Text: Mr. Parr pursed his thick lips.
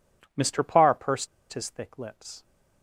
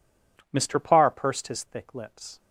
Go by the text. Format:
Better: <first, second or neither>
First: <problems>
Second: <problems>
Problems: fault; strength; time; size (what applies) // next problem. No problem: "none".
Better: second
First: pauses between "pursed" and "his"; slight; at 1.2 s; 0.25 s long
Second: none